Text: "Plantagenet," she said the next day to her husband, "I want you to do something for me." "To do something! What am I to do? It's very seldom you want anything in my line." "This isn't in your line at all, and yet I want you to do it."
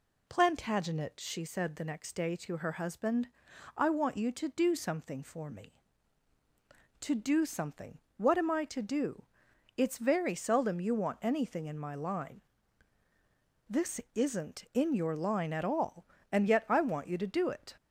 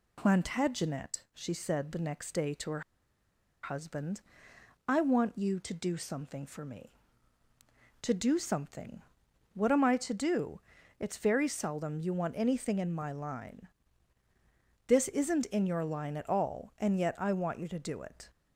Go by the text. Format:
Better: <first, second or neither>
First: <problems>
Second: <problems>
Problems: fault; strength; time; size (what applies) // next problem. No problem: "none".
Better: first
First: none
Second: pauses between "her" and "husband"; noticeable; at 2.8 s; 0.82 s long